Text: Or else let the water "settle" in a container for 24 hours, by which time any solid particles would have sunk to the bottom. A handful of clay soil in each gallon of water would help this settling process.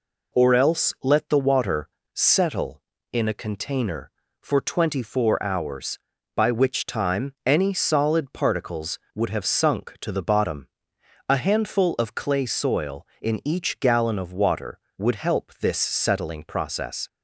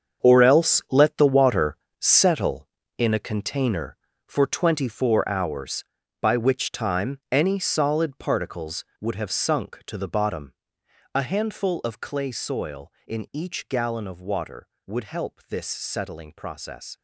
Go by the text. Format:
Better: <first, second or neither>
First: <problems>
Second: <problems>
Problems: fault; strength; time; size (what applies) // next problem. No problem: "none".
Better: first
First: pauses between "water" and "settle"; slight; at 1.8 s; 0.24 s long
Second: gets quieter; strong; throughout; 11 dB // pauses between "water" and "settle"; slight; at 1.7 s; 0.22 s long